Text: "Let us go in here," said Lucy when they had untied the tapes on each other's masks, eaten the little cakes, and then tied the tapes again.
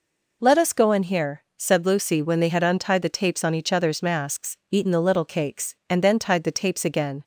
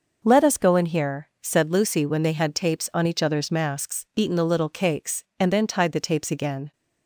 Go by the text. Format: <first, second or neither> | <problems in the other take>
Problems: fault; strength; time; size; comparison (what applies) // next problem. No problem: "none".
first | skips "untied the"; at 2.5 s